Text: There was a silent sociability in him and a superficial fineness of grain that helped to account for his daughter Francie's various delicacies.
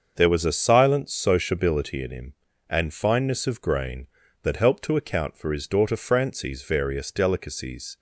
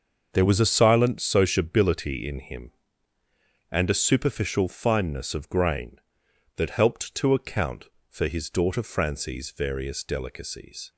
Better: second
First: starts louder than the rest; until 1.1 s; 6.5 dB // skips "a superficial"; at 2.9 s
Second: starts louder than the rest; until 1.3 s; 6.5 dB

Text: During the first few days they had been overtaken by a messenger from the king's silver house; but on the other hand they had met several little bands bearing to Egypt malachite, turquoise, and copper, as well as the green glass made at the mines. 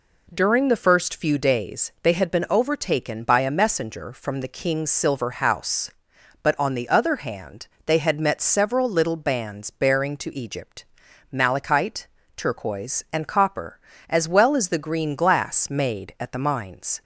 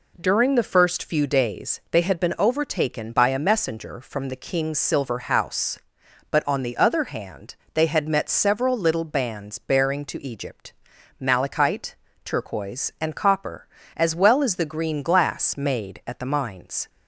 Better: neither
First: pauses between "hand" and "they"; slight; at 7.6 s; 0.18 s long // pauses between "Egypt" and "malachite"; noticeable; at 10.8 s; 0.46 s long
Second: pauses between "hand" and "they"; slight; at 7.5 s; 0.18 s long // pauses between "Egypt" and "malachite"; noticeable; at 10.7 s; 0.46 s long

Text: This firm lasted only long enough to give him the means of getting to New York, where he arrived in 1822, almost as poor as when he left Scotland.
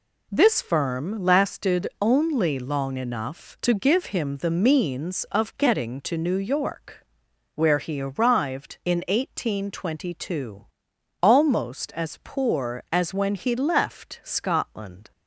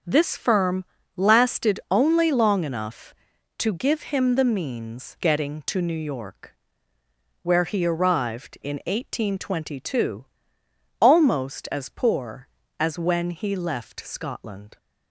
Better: first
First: none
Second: starts louder than the rest; until 1.3 s; 6.5 dB // pauses between "firm" and "lasted"; slight; at 0.8 s; 0.32 s long // skips "of"; at 5.1 s

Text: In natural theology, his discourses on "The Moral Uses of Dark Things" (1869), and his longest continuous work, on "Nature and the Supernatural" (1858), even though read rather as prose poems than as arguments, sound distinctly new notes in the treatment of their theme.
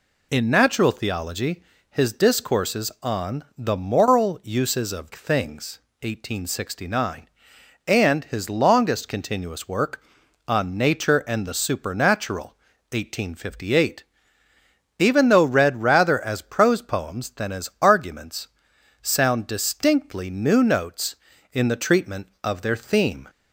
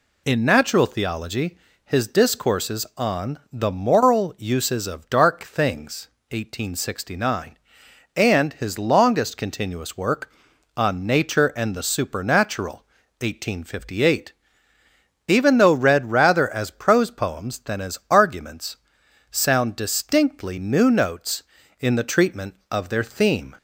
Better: second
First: skips "Dark"; at 5.1 s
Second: none

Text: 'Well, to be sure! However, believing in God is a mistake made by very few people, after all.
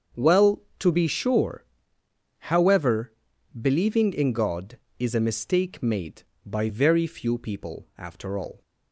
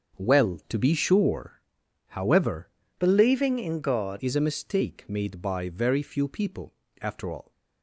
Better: first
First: starts louder than the rest; until 1.3 s; 7 dB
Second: starts louder than the rest; until 1.2 s; 7 dB // changes voice from "believing" to "God"; from 3.0 to 4.1 s; 1.1 s long

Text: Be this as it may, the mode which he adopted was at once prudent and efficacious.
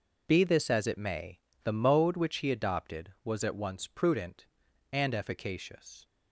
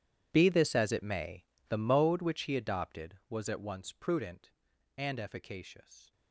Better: first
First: none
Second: gets quieter; strong; throughout; 20.5 dB

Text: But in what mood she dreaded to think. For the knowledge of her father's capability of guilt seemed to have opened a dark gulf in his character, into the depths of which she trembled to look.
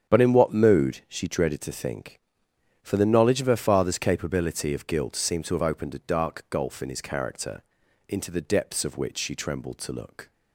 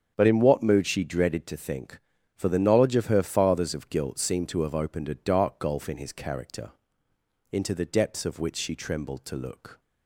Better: first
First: starts louder than the rest; strong; until 1.1 s; 8.5 dB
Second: starts louder than the rest; strong; until 1.1 s; 7.5 dB // skips "capability"; at 3.7 s

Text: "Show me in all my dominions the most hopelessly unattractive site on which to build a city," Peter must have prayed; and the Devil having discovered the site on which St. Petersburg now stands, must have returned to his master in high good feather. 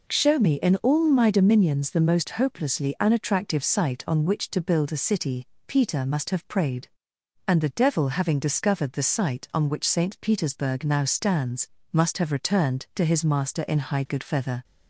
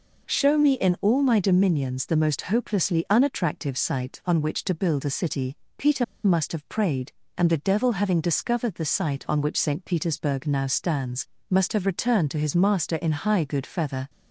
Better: first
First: none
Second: pauses between "Peter" and "must"; slight; at 6.0 s; 0.21 s long

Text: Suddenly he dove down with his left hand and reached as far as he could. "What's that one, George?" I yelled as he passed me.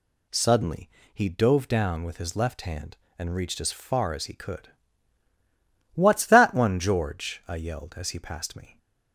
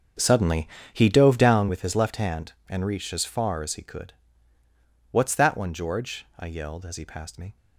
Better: first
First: pauses between "Suddenly" and "he"; slight; at 0.9 s; 0.22 s long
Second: starts louder than the rest; until 1.8 s; 6.5 dB // pauses between "Suddenly" and "he"; slight; at 0.6 s; 0.24 s long

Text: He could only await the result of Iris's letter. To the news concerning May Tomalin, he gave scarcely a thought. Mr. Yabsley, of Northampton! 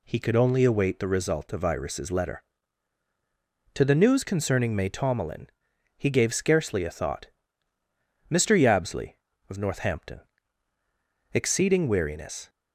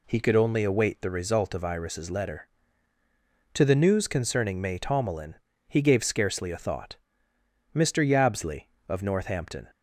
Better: second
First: goes on to say "Exceeding weariness"; noticeable; from 11.3 s on; 1.1 s long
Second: none

